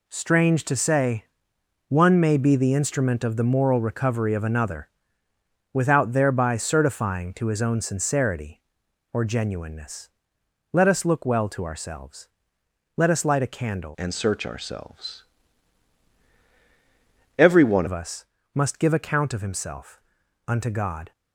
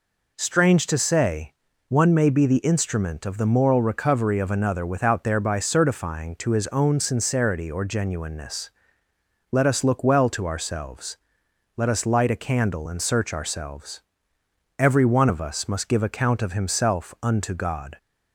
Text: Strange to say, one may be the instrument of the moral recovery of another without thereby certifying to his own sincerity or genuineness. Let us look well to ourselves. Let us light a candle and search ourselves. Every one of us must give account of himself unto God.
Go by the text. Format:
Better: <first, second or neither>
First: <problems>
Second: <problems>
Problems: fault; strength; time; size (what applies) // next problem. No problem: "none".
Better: second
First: pauses between "another" and "without"; noticeable; at 4.8 s; 0.84 s long // changes voice from "and" to "one"; from 13.9 to 17.8 s; 3.9 s long // pauses between "us" and "must"; slight; at 18.2 s; 0.30 s long // pauses between "himself" and "unto"; noticeable; at 19.9 s; 0.48 s long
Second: none